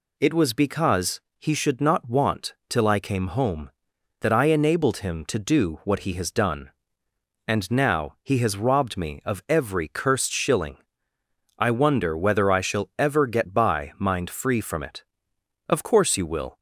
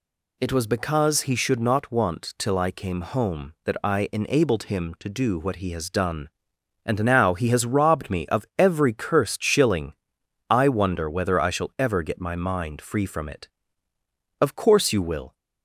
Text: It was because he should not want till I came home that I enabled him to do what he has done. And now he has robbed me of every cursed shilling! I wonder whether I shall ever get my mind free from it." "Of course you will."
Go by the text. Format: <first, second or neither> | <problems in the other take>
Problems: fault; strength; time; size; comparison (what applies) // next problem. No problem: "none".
second | pauses between "because" and "he"; slight; at 1.1 s; 0.20 s long // says "by" for "my"; at 13.5 s